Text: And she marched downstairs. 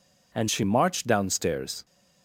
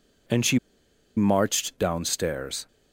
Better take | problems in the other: first | pauses between "she" and "marched"; noticeable; at 0.5 s; 0.58 s long

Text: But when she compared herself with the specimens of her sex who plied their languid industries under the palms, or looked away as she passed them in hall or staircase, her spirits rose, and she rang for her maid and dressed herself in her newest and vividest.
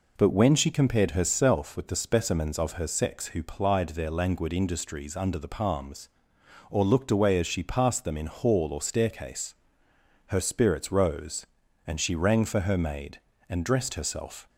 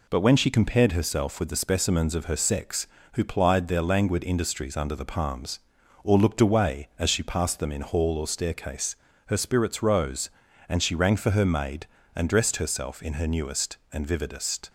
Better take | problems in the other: second | stops before "in her newest and vividest"; at 14.4 s

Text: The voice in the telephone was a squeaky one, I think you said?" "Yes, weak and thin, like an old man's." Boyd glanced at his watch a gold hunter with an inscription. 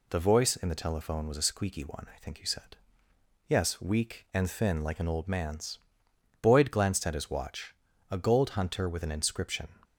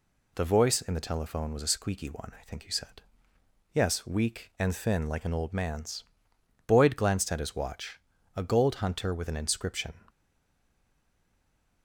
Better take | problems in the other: first | pauses between "watch" and "a"; slight; at 8.0 s; 0.34 s long; slight in the first // stays silent after the last word; noticeable; from 10.0 s on; 1.8 s long

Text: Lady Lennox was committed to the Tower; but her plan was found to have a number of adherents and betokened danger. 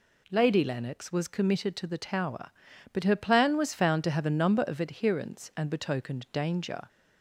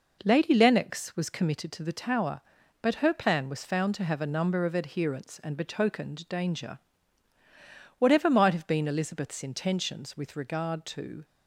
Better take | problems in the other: first | goes on to say "Whatever might have been Elizabeth's intentions with regard to"; strong; from 7.9 s on; 3.2 s long

